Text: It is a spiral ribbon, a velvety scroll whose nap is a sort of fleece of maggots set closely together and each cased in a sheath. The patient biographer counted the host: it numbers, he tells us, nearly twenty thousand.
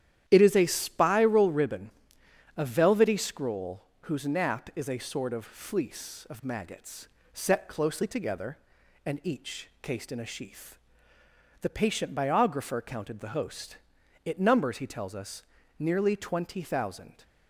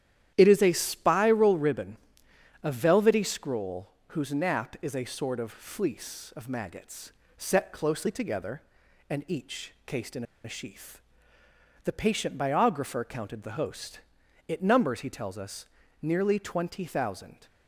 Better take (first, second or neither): first